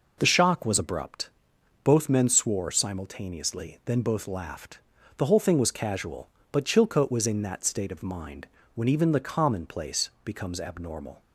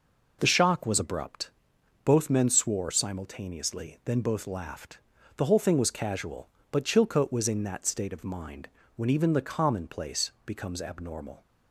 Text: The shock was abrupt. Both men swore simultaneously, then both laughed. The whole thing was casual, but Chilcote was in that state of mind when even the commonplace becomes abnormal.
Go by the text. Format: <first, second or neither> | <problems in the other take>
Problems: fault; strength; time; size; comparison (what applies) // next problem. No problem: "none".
neither | pauses between "mind" and "when"; slight; the same in both // pauses between "commonplace" and "becomes"; slight; the same in both